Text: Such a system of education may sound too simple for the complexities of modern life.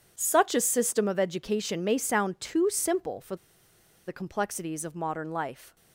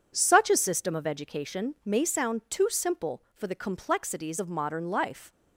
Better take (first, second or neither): second